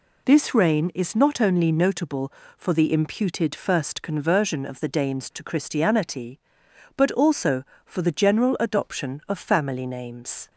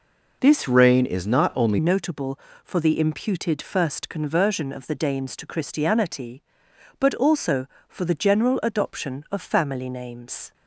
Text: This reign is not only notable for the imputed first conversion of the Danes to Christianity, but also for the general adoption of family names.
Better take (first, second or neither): first